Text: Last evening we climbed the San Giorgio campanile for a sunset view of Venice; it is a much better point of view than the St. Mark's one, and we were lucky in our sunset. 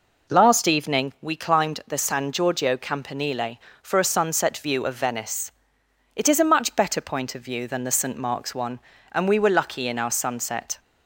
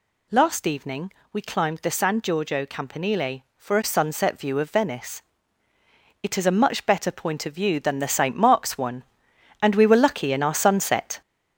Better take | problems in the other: first | gets louder; noticeable; throughout; 5.5 dB // pauses between "evening" and "we"; slight; at 1.0 s; 0.22 s long

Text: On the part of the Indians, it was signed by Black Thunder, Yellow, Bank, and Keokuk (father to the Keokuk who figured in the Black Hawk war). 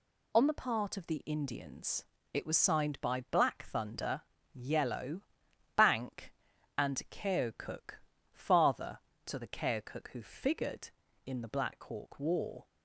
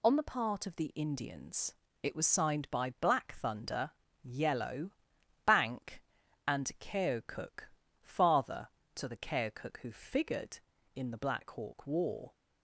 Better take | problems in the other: neither | none

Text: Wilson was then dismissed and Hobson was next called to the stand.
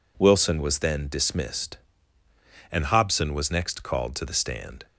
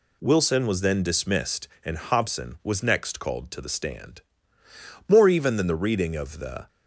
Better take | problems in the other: first | goes on to say "More even than the reading of the"; from 5.0 s on; 1.6 s long

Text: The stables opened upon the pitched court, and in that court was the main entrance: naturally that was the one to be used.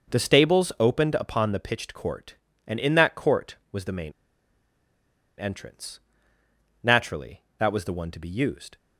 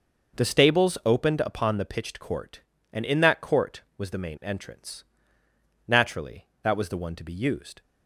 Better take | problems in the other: second | pauses between "main" and "entrance"; strong; at 4.1 s; 1.2 s long

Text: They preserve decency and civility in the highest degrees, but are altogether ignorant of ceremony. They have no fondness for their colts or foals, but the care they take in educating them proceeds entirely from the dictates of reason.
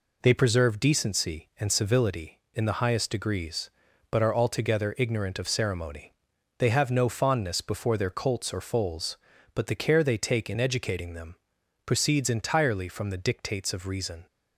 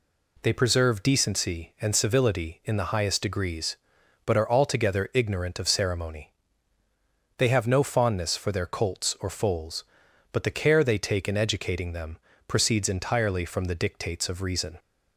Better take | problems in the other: second | says "before" for "for"; at 7.6 s // pauses between "them" and "proceeds"; noticeable; at 11.3 s; 0.50 s long; slight in the second

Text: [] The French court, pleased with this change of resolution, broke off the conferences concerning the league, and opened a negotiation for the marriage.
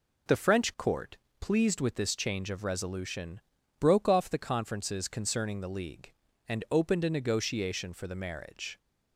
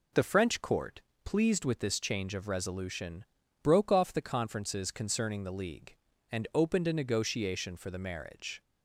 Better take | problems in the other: neither | none

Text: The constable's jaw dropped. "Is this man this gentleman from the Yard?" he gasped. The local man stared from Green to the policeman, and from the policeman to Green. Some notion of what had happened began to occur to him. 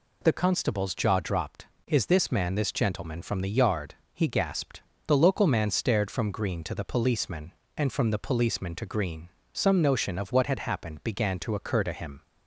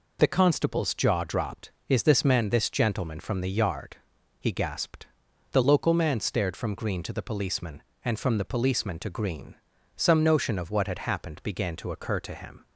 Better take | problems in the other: neither | none

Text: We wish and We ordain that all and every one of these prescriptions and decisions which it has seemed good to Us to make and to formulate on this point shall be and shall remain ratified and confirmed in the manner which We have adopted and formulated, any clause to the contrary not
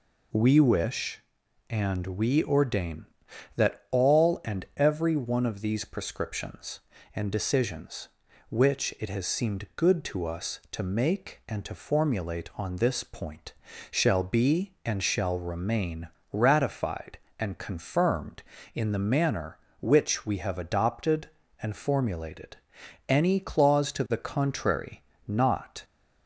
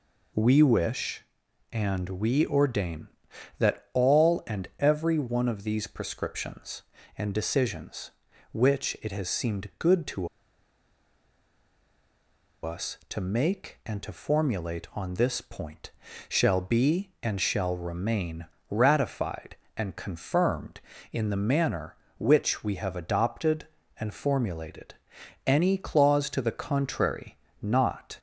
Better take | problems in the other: first | pauses between "to" and "Us"; strong; at 10.2 s; 2.3 s long // pauses between "point" and "shall"; at 15.9 s; 0.38 s long; also in the first // pauses between "remain" and "ratified"; slight; at 18.4 s; 0.24 s long; slight in the first // pauses between "contrary" and "not"; slight; at 27.3 s; 0.26 s long; slight in the first

